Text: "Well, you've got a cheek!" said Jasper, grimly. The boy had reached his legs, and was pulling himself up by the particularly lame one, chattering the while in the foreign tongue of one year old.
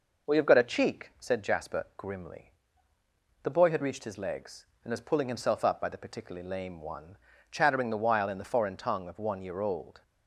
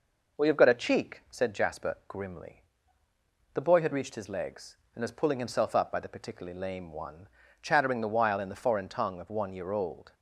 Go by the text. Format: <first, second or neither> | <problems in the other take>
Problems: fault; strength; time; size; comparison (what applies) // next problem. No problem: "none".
neither | none